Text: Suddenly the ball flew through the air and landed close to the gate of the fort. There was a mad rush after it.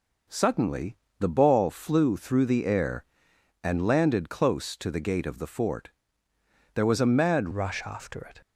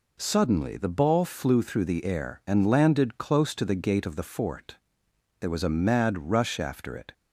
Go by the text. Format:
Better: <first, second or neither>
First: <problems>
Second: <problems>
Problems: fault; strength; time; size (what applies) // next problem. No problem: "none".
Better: second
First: pauses between "Suddenly" and "the"; slight; at 0.9 s; 0.24 s long // changes voice at "rush"; from 7.5 s on; 0.9 s long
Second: none